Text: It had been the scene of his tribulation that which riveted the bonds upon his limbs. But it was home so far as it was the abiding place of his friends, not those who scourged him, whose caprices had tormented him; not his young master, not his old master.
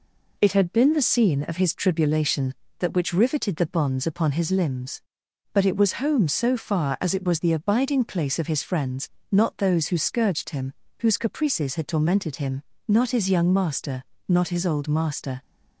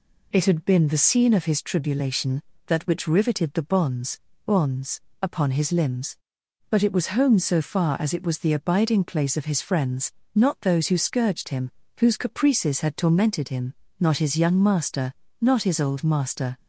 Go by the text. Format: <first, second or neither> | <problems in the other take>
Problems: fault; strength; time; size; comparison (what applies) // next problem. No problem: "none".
first | says "bonds" twice; at 4.4 s